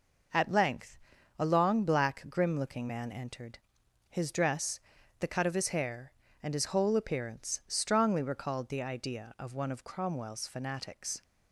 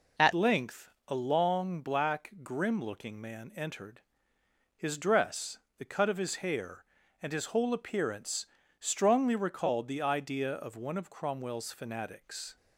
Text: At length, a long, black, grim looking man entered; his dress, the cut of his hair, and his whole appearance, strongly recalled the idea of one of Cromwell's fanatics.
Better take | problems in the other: first | changes voice at "length"; from 0.3 s on; 12.2 s long

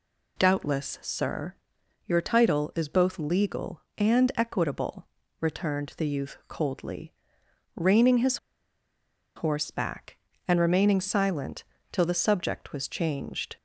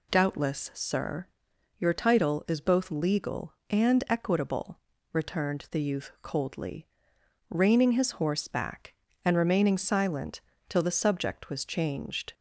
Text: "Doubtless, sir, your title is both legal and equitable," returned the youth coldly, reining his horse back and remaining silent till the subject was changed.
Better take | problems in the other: second | pauses between "his" and "horse"; at 8.3 s; 0.98 s long // pauses between "silent" and "till"; slight; at 11.6 s; 0.26 s long; slight in the second

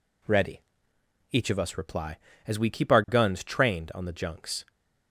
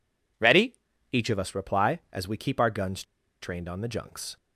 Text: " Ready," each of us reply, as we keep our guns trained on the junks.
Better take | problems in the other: first | pauses between "guns" and "trained"; at 3.0 s; 0.37 s long

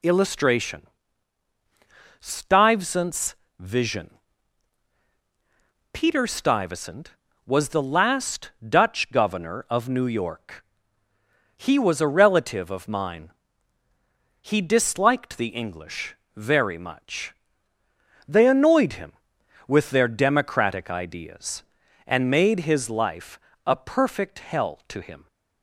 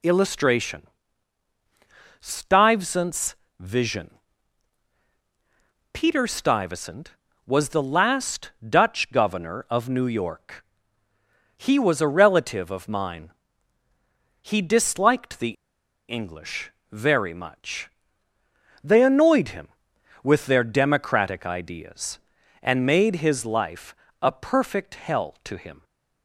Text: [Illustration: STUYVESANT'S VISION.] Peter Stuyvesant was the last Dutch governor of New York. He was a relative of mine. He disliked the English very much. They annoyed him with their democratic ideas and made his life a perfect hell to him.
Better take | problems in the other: first | pauses between "STUYVESANT'S" and "VISION"; slight; at 3.3 s; 0.24 s long; slight in the first // pauses between "the" and "English"; noticeable; at 15.5 s; 0.56 s long // pauses between "English" and "very"; slight; at 16.6 s; 0.22 s long; slight in the first // pauses between "life" and "a"; slight; at 23.9 s; 0.26 s long; slight in the first

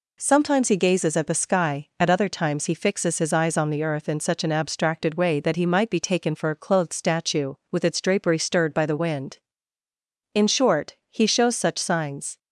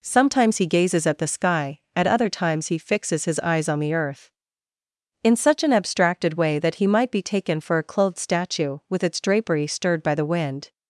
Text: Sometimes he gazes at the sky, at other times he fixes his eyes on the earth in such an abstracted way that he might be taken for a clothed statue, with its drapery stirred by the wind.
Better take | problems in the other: second | goes on to say "In short he shows such signs"; strong; from 10.3 s on; 2.0 s long

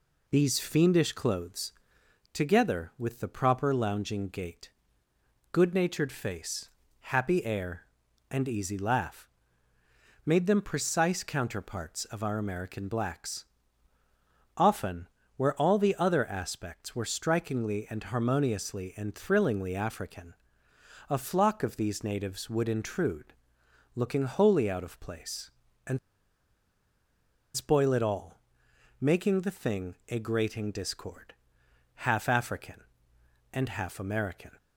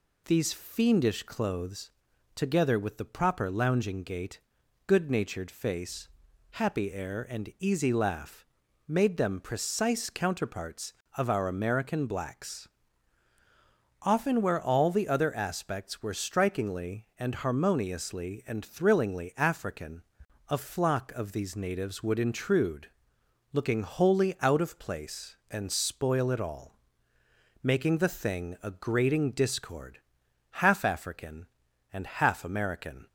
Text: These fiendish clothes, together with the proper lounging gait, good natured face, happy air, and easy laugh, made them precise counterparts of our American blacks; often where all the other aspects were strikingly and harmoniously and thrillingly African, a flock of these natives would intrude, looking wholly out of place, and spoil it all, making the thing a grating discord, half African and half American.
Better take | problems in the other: second | pauses between "often" and "where"; slight; at 15.0 s; 0.30 s long // pauses between "and" and "spoil"; strong; at 25.9 s; 1.5 s long

